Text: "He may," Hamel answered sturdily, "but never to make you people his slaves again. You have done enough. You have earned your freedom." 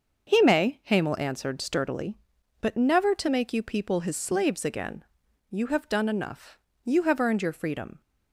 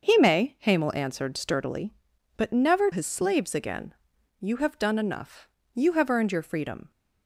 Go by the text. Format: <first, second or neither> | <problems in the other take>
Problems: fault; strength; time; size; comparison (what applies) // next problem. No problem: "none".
first | starts louder than the rest; until 1.1 s; 6 dB; also in the first // skips "to make you people"; at 2.9 s